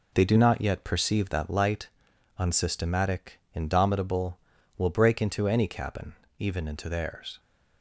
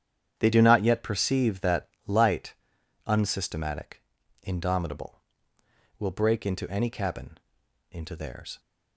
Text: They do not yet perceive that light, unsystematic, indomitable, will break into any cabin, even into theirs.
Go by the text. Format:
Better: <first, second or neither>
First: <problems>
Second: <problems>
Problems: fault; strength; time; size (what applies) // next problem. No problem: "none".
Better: first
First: none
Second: starts louder than the rest; strong; until 1.3 s; 9 dB // pauses between "that" and "light"; slight; at 1.8 s; 0.18 s long // skips "even"; at 7.6 s